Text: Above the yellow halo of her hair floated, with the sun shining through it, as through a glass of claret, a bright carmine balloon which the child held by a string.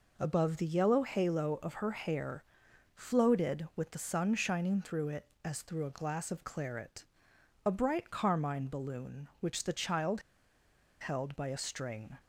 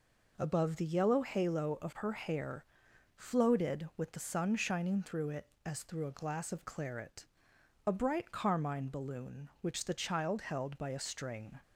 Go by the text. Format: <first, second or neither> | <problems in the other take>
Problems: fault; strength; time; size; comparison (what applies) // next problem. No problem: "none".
second | pauses between "hair" and "floated"; noticeable; at 2.4 s; 0.52 s long; noticeable in the second // pauses between "child" and "held"; noticeable; at 10.2 s; 0.79 s long